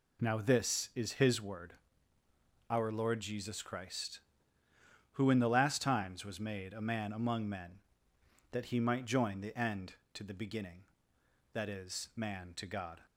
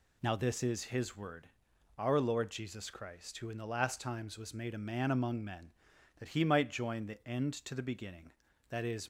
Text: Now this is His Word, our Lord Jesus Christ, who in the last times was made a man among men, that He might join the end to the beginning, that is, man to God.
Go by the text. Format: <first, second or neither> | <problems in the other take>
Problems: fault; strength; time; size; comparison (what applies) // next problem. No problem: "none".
first | stops before "man to God"; at 9.0 s